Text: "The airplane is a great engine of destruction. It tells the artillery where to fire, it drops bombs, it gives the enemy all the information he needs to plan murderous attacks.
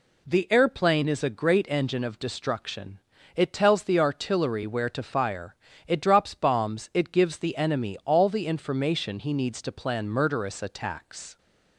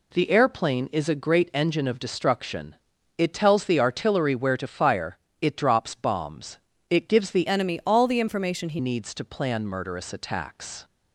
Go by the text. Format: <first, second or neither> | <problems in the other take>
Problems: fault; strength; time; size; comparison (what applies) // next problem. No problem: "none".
first | changes voice from "enemy" to "he"; from 7.4 to 8.7 s; 1.3 s long